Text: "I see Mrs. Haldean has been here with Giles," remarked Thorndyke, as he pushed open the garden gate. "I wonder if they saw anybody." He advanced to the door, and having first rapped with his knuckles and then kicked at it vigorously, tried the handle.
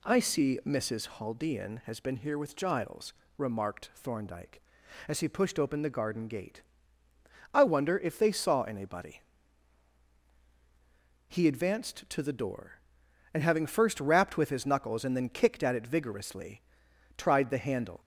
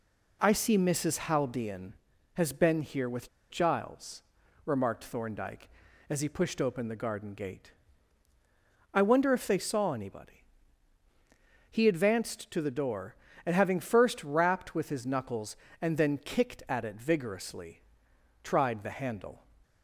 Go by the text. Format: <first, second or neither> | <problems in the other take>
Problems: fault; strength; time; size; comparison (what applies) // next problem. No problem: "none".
first | pauses between "with" and "Giles"; slight; at 3.2 s; 0.21 s long